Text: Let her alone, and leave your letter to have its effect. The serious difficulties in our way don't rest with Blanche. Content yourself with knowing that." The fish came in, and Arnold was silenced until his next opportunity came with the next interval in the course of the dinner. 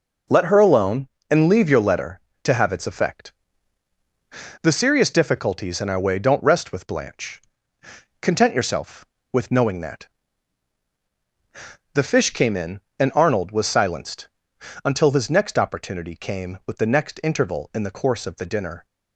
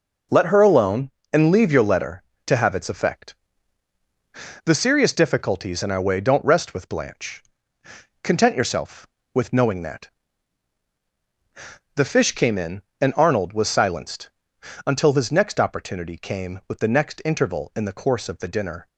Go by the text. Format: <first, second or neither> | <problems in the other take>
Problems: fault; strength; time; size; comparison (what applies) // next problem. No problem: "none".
neither | pauses between "silenced" and "until"; noticeable; the same in both